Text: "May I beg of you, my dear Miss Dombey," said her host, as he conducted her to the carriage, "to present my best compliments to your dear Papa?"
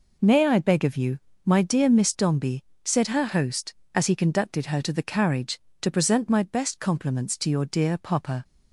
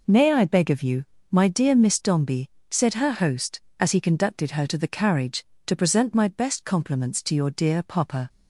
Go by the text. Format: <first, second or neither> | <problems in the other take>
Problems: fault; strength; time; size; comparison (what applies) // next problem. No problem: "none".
neither | none